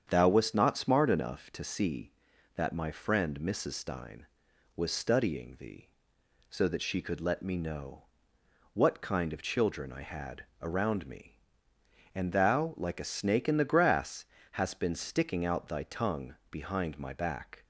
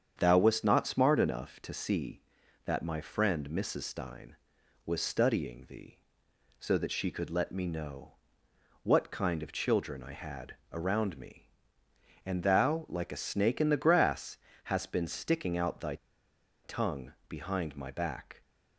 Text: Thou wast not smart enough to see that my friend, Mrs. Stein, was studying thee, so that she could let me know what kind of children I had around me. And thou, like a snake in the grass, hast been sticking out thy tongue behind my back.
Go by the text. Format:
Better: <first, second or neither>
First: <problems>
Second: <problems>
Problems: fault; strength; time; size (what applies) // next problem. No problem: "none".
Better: first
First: starts louder than the rest; strong; until 1.1 s; 8 dB // pauses between "know" and "what"; noticeable; at 8.0 s; 0.68 s long // pauses between "had" and "around"; slight; at 10.4 s; 0.18 s long // pauses between "tongue" and "behind"; slight; at 16.3 s; 0.16 s long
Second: starts louder than the rest; strong; until 1.2 s; 8 dB // pauses between "know" and "what"; noticeable; at 8.1 s; 0.68 s long // pauses between "had" and "around"; slight; at 10.5 s; 0.18 s long // pauses between "thy" and "tongue"; noticeable; at 15.9 s; 0.68 s long // pauses between "tongue" and "behind"; slight; at 17.1 s; 0.16 s long